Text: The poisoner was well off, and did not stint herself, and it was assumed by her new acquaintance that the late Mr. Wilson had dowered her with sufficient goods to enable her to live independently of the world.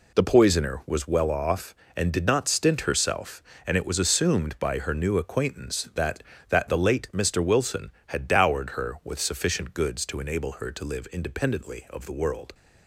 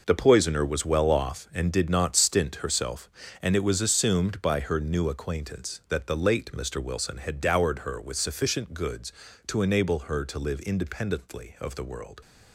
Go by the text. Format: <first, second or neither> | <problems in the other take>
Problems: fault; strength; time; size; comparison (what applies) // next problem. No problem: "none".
second | says "that" twice; at 6.4 s